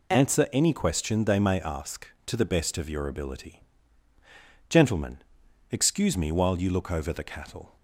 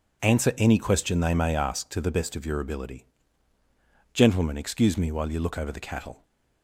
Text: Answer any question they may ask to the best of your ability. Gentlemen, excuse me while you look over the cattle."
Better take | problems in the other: neither | none

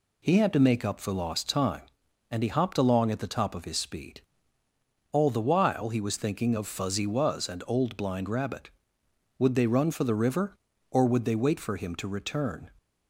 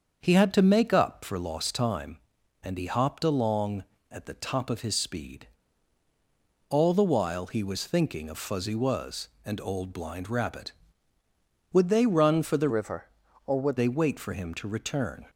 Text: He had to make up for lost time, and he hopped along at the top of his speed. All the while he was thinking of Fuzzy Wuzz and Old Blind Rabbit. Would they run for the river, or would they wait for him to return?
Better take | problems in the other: first | starts louder than the rest; until 1.2 s; 7 dB // changes voice from "river" to "would"; from 12.6 to 13.7 s; 1.1 s long

